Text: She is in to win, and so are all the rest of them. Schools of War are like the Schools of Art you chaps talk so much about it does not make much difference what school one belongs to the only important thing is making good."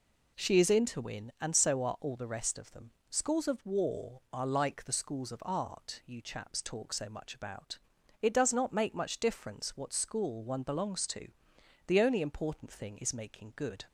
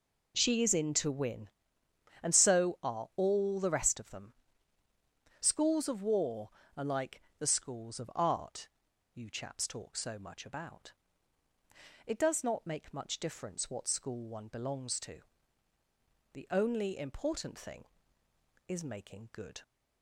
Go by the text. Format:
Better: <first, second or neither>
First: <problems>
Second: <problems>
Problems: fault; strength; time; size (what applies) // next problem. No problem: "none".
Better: first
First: pauses between "about" and "it"; at 7.7 s; 0.42 s long // pauses between "to" and "the"; noticeable; at 11.2 s; 0.60 s long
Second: pauses between "like" and "the"; slight; at 7.2 s; 0.16 s long // pauses between "Art" and "you"; noticeable; at 8.6 s; 0.46 s long // pauses between "about" and "it"; at 10.9 s; 1.1 s long // pauses between "to" and "the"; at 15.1 s; 1.1 s long